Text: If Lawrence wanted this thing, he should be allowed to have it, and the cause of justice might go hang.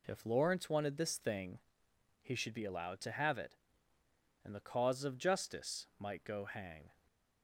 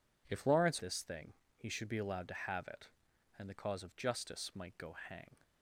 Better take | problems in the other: first | skips "wanted"; at 0.8 s

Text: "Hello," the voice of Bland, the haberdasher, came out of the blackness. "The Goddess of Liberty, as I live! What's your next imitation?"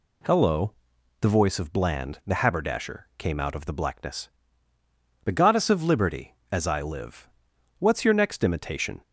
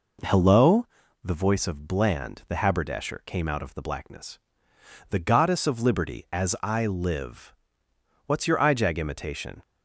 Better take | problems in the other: first | says "ijag" for "next"; at 8.5 s

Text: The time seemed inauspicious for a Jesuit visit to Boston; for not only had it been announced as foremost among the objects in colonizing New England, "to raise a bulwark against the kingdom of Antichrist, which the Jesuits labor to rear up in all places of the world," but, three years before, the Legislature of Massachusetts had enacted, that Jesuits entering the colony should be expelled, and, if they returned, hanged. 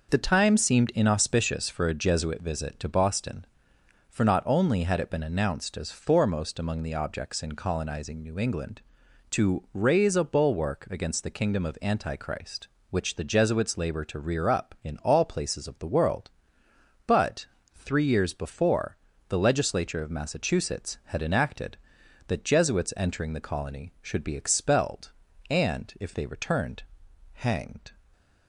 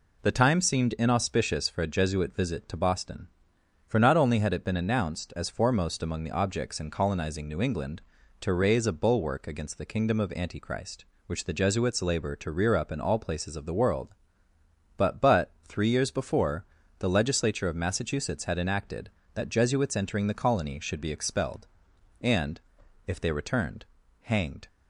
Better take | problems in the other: first | says "but" twice; at 15.2 s

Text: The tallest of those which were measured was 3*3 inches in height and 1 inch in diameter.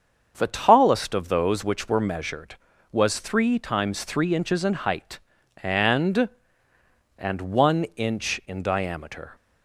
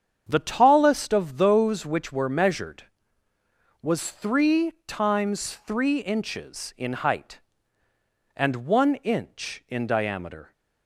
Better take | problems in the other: second | starts louder than the rest; until 1.3 s; 6.5 dB; strong in the second // says "and" twice; at 7.1 s

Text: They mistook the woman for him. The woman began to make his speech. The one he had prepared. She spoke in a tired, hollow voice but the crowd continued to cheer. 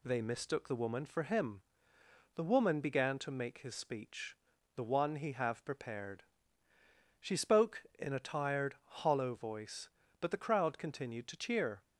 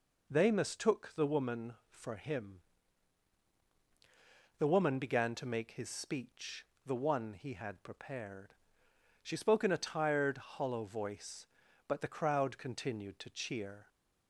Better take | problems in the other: second | says "have" for "had"; at 5.3 s

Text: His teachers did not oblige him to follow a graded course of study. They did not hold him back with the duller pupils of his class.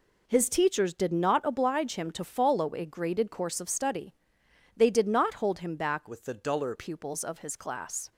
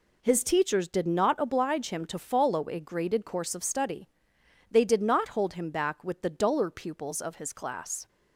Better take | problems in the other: second | changes voice from "with" to "duller"; from 6.0 to 6.7 s; 0.7 s long

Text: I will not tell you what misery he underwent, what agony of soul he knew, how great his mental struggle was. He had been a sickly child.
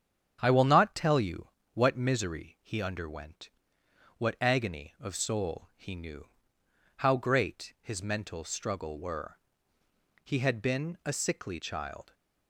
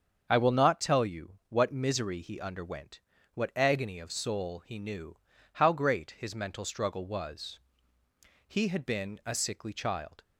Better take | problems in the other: second | starts louder than the rest; strong; until 1.4 s; 8 dB; also in the second // pauses between "you" and "what"; slight; at 1.4 s; 0.26 s long // says "were" for "was"; at 8.9 s

